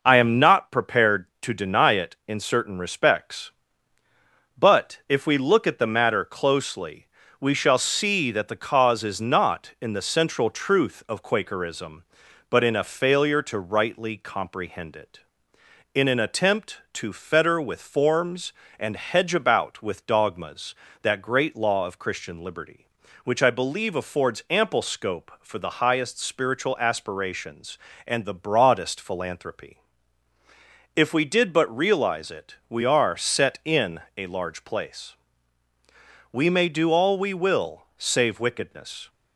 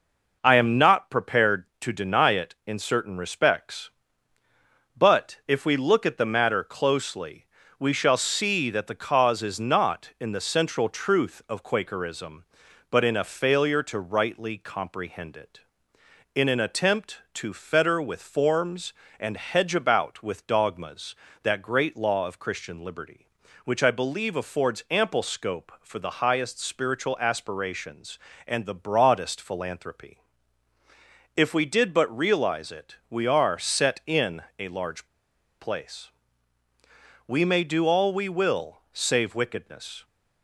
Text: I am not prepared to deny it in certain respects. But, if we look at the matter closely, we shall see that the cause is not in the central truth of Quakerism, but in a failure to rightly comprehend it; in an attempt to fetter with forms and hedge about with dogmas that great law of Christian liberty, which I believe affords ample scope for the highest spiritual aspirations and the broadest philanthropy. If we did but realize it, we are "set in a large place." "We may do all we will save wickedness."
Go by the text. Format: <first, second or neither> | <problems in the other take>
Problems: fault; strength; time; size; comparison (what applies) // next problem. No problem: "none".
first | pauses between "in" and "a"; slight; at 34.4 s; 0.16 s long; slight in the first // pauses between "large" and "place"; noticeable; at 35.0 s; 0.56 s long